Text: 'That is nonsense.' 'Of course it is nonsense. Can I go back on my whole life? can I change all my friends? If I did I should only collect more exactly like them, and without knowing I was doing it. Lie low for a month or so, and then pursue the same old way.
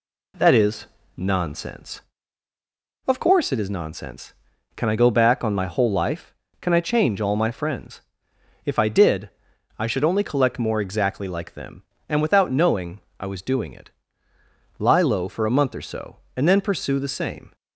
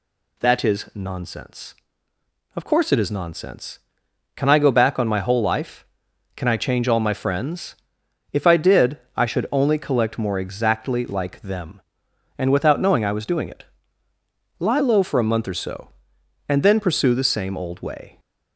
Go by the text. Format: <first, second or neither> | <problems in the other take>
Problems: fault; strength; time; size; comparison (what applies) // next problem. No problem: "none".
second | pauses between "is" and "nonsense"; slight; at 0.8 s; 0.30 s long // pauses between "did" and "I"; noticeable; at 9.2 s; 0.50 s long; slight in the second // pauses between "knowing" and "I"; slight; at 12.9 s; 0.18 s long // stops before "old way"; at 17.5 s